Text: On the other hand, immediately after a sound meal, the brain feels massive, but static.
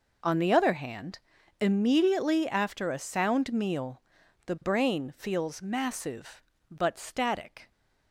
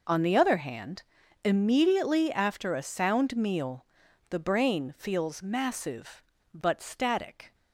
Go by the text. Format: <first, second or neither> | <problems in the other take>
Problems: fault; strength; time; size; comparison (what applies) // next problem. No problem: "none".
neither | none